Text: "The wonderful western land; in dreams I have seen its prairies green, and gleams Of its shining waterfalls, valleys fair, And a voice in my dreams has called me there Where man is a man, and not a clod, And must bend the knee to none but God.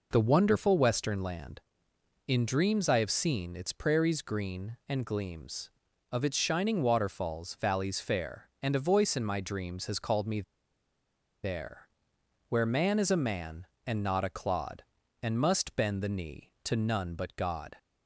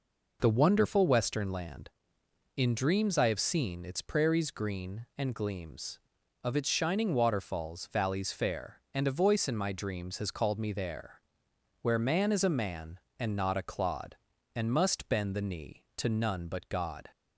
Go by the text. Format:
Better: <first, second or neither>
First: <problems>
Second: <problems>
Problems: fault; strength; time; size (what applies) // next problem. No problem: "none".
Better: second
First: pauses between "me" and "there"; at 10.4 s; 1.0 s long // pauses between "there" and "Where"; noticeable; at 11.8 s; 0.58 s long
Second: pauses between "there" and "Where"; noticeable; at 11.2 s; 0.58 s long